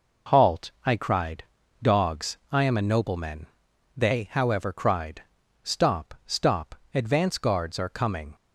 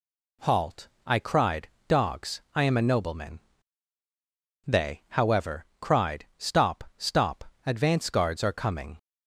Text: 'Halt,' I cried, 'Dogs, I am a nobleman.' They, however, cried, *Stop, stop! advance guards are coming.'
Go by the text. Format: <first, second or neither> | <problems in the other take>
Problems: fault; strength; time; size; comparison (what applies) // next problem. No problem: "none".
neither | none